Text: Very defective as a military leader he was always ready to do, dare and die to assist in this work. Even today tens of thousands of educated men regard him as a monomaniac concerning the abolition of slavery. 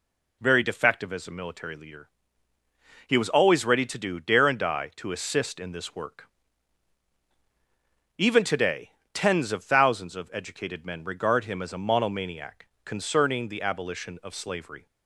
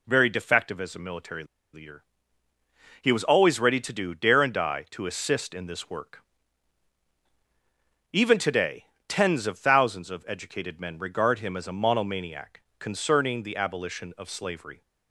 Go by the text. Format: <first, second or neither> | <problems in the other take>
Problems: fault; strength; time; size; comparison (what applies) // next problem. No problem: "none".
first | pauses between "military" and "leader"; slight; at 1.4 s; 0.28 s long // pauses between "leader" and "he"; noticeable; at 2.0 s; 0.96 s long; noticeable in the first // pauses between "today" and "tens"; slight; at 8.8 s; 0.22 s long; slight in the first // pauses between "monomaniac" and "concerning"; slight; at 12.6 s; 0.18 s long; slight in the first